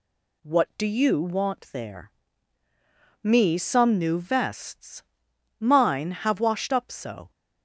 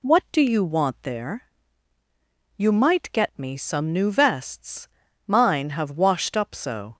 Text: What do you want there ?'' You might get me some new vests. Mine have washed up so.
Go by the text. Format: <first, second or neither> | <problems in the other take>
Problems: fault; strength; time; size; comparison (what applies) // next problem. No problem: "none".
second | skips "You might get"; at 3.2 s